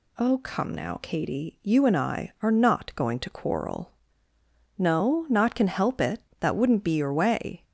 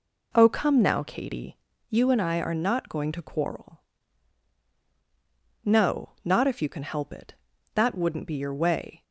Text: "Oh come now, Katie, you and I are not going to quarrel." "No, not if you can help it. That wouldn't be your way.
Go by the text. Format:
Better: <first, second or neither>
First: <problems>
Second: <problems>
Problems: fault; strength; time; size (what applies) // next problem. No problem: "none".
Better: second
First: skips "if you"; at 5.5 s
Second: none